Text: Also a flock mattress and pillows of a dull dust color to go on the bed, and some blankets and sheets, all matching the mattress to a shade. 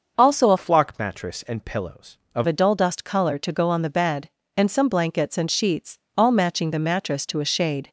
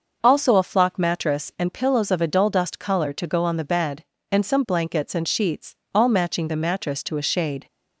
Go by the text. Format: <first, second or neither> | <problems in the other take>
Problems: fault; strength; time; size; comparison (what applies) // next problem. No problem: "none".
second | starts louder than the rest; noticeable; until 1.1 s; 6 dB // changes voice from "flock" to "of"; from 0.5 to 2.4 s; 1.9 s long